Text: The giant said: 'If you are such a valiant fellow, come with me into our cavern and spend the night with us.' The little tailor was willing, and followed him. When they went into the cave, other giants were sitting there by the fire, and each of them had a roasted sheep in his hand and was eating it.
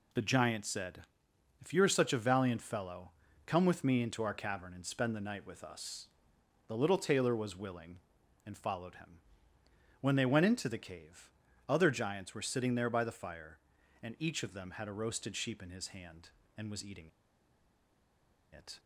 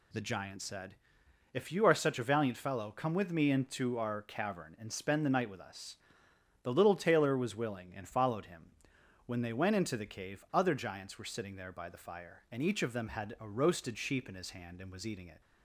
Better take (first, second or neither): second